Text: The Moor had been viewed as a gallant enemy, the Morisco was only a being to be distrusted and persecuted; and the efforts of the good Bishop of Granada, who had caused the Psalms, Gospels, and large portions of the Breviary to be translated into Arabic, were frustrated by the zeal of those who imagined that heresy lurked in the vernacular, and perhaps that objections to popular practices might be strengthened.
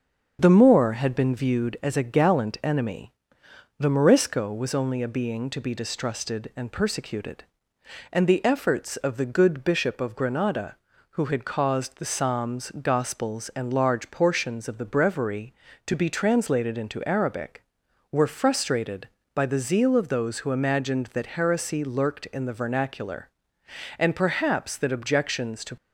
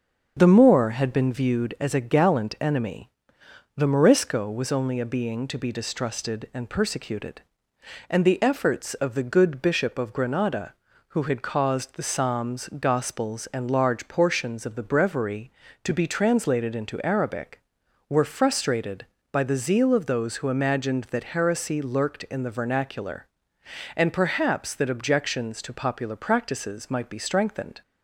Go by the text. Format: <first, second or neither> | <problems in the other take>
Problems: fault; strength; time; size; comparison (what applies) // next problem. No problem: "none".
second | starts louder than the rest; until 1.4 s; 7 dB; also in the second // stops before "popular practices might be strengthened"; at 25.7 s